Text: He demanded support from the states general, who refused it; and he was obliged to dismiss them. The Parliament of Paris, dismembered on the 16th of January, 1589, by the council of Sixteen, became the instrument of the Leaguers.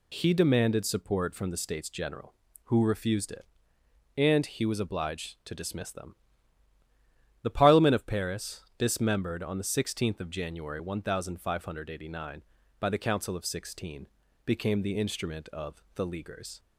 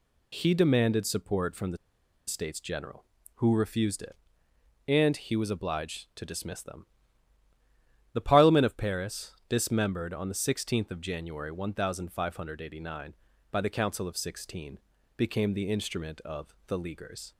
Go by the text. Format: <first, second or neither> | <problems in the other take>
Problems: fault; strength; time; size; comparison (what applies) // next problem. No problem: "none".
first | pauses between "the" and "states"; noticeable; at 1.7 s; 0.50 s long